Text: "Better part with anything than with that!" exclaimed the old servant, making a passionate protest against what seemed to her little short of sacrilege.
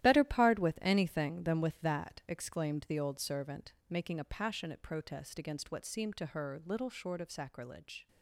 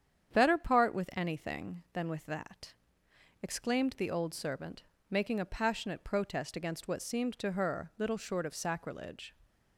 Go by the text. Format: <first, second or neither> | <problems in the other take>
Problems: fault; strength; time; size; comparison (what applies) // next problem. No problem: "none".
second | gets quieter; strong; throughout; 11 dB // starts louder than the rest; strong; until 1.0 s; 13 dB; strong in the second